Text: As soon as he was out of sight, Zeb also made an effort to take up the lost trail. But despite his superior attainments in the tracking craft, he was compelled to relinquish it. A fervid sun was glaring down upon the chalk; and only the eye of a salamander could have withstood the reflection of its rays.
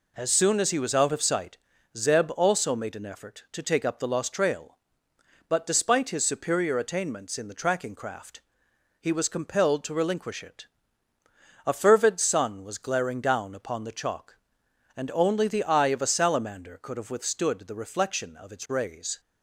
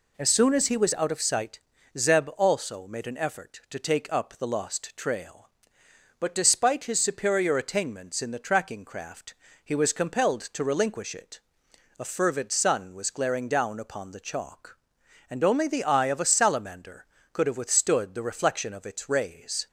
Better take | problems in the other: neither | none

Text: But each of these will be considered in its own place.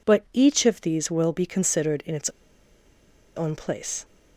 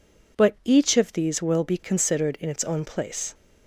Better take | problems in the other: second | pauses between "its" and "own"; at 2.2 s; 1.0 s long

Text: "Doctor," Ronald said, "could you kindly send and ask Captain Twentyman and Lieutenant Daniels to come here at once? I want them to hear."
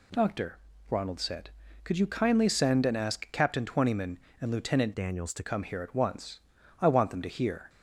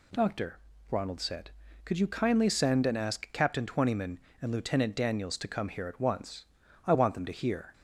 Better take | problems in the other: second | changes voice from "Daniels" to "to"; from 4.9 to 5.4 s; 0.5 s long

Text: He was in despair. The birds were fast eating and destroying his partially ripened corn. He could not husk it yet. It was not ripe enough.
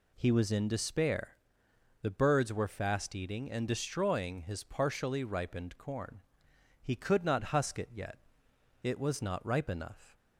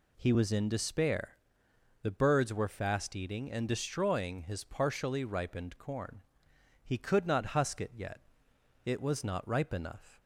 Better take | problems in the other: neither | none

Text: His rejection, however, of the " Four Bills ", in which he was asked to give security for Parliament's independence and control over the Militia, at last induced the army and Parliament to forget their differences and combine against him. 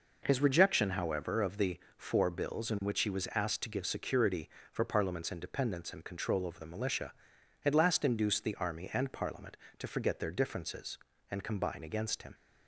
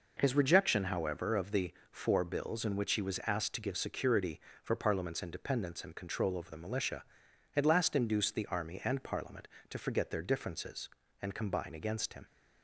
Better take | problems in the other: neither | none

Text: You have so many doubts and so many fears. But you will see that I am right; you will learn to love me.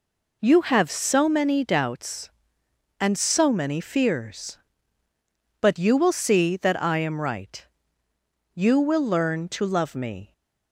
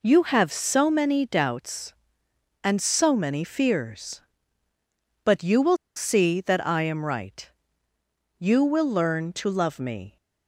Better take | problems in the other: first | pauses between "will" and "see"; slight; at 5.7 s; 0.19 s long

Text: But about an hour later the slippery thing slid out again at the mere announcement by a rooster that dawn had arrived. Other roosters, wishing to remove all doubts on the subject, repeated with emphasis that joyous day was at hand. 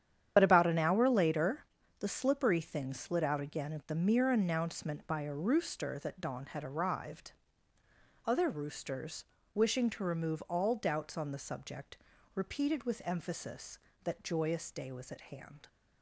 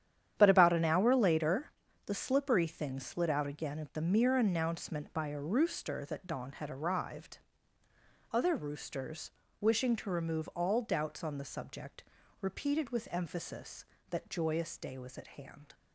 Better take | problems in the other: second | loses the start of "But"; at 0.3 s; 50 ms // starts louder than the rest; strong; until 1.3 s; 9.5 dB; strong in the second // pauses between "later" and "the"; slight; at 1.6 s; 0.34 s long; slight in the second

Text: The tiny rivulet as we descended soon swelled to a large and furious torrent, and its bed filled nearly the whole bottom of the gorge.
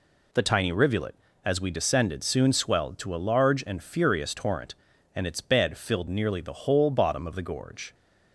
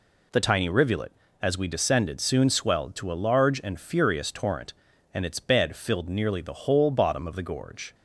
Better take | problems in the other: neither | none

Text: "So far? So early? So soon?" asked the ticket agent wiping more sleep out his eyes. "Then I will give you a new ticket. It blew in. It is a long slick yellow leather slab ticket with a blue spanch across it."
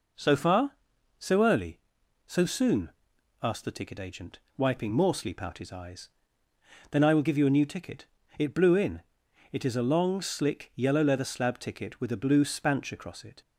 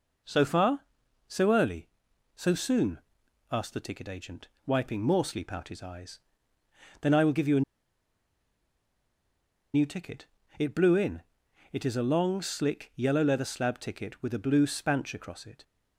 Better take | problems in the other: first | pauses between "agent" and "wiping"; slight; at 4.4 s; 0.18 s long; slight in the first // pauses between "a" and "new"; strong; at 7.6 s; 2.1 s long

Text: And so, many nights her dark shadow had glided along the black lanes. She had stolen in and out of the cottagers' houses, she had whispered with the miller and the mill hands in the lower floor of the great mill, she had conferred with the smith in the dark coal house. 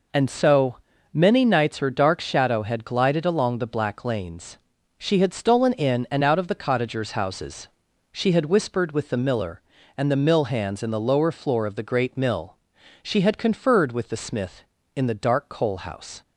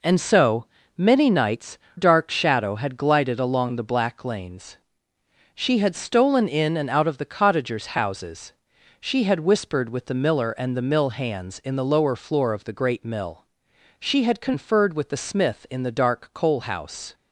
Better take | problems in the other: first | skips "her"; at 1.8 s

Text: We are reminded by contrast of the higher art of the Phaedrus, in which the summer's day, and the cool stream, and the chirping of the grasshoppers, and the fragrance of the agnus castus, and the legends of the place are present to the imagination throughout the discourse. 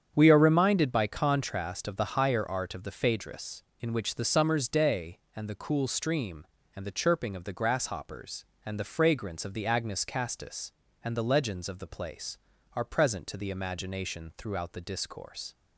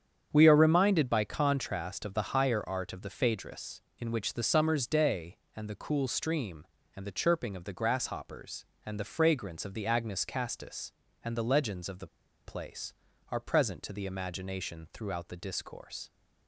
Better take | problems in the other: first | starts louder than the rest; strong; until 1.3 s; 8 dB; strong in the first // pauses between "the" and "place"; at 12.0 s; 0.37 s long

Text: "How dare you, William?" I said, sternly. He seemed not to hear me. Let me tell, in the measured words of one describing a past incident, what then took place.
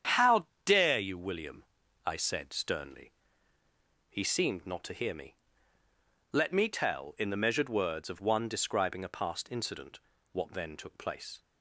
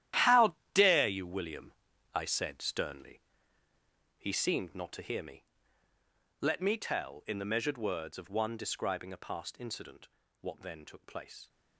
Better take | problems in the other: first | gets quieter; strong; throughout; 13 dB // starts louder than the rest; strong; until 1.3 s; 12 dB; strong in the first // pauses between "How" and "dare"; slight; at 0.5 s; 0.20 s long; slight in the first

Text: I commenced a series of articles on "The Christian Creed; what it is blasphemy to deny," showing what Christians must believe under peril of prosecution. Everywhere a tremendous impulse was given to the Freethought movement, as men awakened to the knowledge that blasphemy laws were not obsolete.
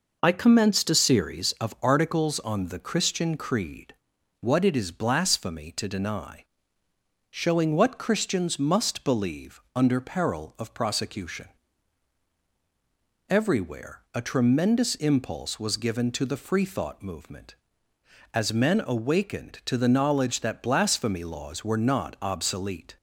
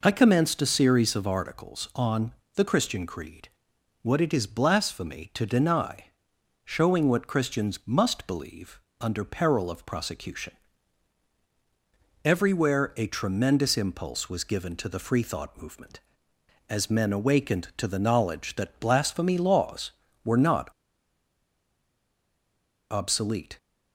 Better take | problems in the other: first | pauses between "on" and "The"; slight; at 2.3 s; 0.22 s long // pauses between "believe" and "under"; slight; at 8.7 s; 0.22 s long; slight in the first // pauses between "not" and "obsolete"; strong; at 20.6 s; 2.2 s long

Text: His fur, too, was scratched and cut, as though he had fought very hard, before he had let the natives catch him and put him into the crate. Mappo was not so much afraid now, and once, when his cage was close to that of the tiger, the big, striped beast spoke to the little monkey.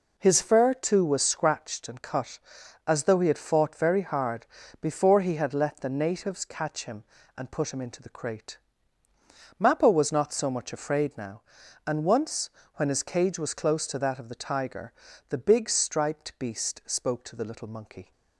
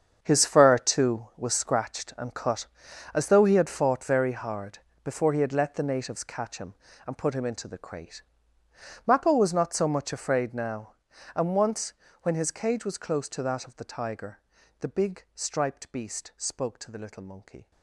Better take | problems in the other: first | gets quieter; strong; throughout; 14.5 dB

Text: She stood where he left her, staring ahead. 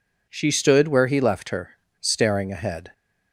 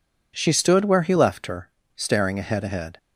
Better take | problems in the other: first | says "ahead" twice; at 2.6 s

